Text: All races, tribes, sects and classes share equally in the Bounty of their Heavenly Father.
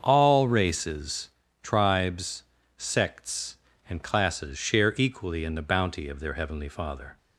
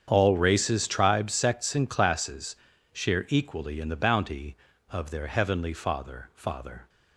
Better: first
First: starts louder than the rest; until 1.0 s; 7 dB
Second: starts louder than the rest; strong; until 1.0 s; 8 dB // pauses between "classes" and "share"; at 2.5 s; 0.38 s long // says "Father" twice; at 6.3 s

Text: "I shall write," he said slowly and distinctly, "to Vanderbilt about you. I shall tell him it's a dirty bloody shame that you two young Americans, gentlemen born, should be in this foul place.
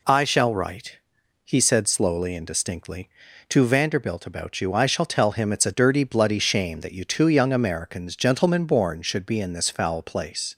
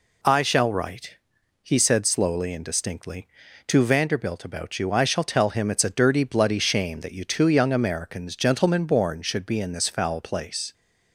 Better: neither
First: none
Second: none

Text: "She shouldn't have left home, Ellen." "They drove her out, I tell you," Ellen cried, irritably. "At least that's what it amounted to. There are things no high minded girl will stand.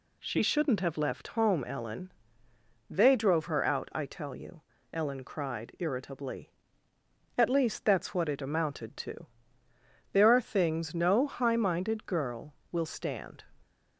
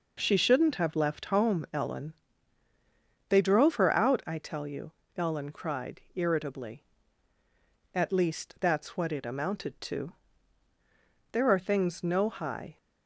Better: first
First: none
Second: stops before "minded girl will stand"; at 12.7 s

